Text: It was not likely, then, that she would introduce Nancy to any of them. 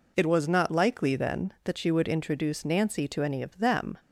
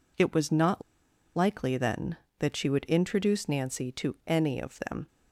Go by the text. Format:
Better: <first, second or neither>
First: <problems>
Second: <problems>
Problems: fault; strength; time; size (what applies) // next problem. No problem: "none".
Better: first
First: none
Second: pauses between "not" and "likely"; noticeable; at 0.8 s; 0.54 s long